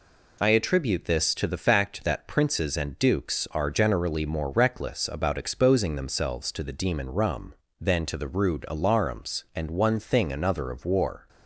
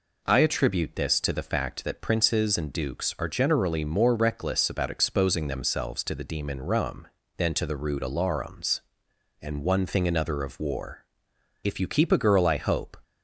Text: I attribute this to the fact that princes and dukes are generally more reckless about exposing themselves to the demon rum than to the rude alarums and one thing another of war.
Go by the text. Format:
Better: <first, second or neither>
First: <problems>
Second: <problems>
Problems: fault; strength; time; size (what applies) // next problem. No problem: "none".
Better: first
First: none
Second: goes on to say "If you keep a girl I hope"; from 11.6 s on; 1.3 s long